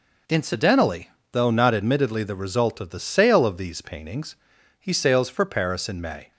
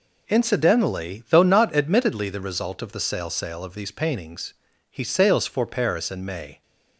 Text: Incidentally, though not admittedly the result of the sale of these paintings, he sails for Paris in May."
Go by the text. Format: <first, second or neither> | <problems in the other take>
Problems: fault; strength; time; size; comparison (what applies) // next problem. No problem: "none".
first | says "sale" twice; at 3.2 s